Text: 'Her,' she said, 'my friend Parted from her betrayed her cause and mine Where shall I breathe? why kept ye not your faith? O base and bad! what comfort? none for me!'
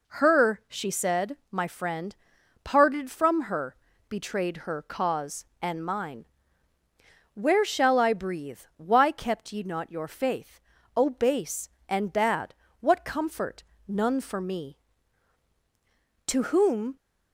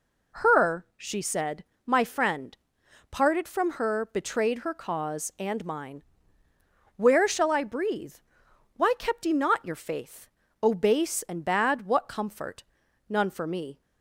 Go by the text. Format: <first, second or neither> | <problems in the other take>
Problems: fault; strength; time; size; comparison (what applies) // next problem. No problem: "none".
second | pauses between "friend" and "Parted"; noticeable; at 2.1 s; 0.48 s long; noticeable in the second // pauses between "her" and "betrayed"; slight; at 3.7 s; 0.34 s long // pauses between "mine" and "Where"; at 6.2 s; 1.0 s long; noticeable in the second // goes on to say "To whom"; noticeable; from 16.2 s on; 0.68 s long